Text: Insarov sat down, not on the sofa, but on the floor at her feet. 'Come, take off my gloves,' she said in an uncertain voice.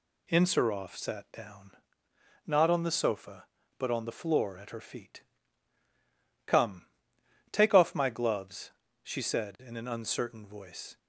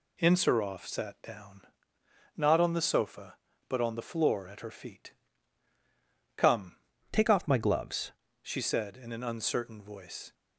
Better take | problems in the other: first | changes voice from "take" to "gloves"; from 7.1 to 8.1 s; 1.0 s long

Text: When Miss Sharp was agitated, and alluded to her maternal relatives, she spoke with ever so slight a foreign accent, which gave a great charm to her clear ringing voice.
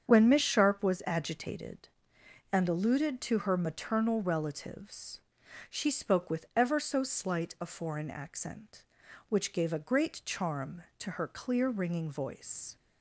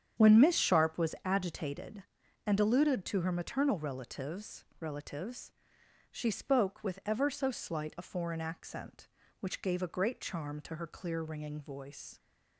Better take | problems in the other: first | starts louder than the rest; strong; until 1.2 s; 8.5 dB; strong in the first // says "relatives" twice; at 4.7 s

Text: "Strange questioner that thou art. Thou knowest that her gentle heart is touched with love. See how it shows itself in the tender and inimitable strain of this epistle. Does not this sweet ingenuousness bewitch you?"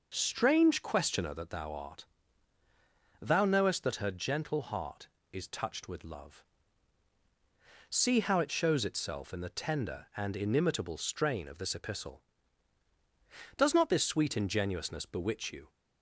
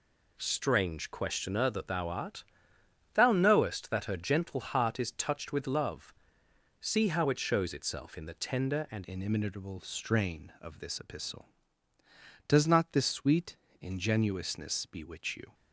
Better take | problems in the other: first | changes voice at "inimitable"; from 9.0 s on; 6.5 s long // pauses between "sweet" and "ingenuousness"; slight; at 13.5 s; 0.24 s long

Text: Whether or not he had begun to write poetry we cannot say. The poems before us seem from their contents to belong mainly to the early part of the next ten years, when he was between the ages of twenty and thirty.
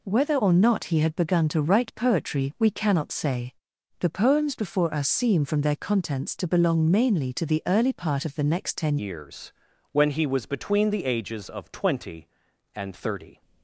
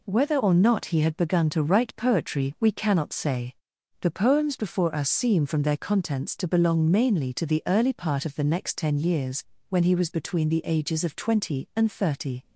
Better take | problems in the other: second | changes voice at "years"; from 8.9 s on; 4.5 s long

